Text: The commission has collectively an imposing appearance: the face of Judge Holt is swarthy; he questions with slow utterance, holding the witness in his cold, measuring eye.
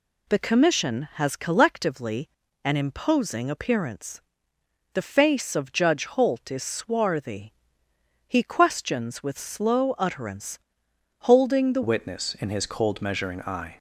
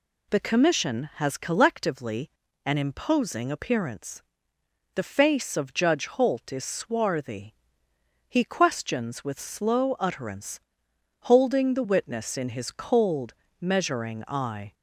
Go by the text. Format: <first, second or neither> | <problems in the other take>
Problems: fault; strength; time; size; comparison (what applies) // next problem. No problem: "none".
second | pauses between "collectively" and "an"; slight; at 2.2 s; 0.36 s long; slight in the second // changes voice at "witness"; from 11.8 s on; 1.9 s long